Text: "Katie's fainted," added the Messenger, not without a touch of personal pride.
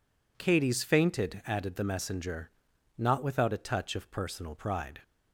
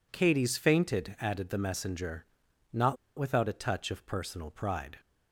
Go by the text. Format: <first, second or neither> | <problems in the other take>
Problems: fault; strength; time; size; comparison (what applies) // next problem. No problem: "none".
first | pauses between "not" and "without"; slight; at 2.9 s; 0.20 s long